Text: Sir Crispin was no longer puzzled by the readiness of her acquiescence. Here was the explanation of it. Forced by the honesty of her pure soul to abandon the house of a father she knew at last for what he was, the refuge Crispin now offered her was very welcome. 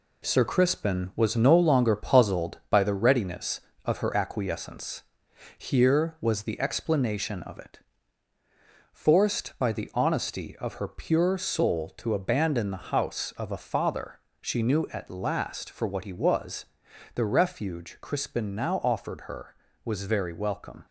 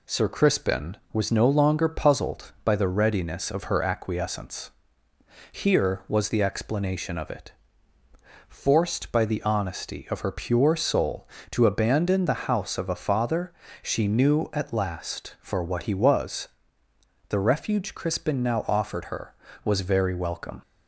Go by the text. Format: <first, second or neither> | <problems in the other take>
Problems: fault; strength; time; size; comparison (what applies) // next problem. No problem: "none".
second | gets quieter; noticeable; throughout; 6 dB // pauses between "father" and "she"; slight; at 14.1 s; 0.20 s long; slight in the second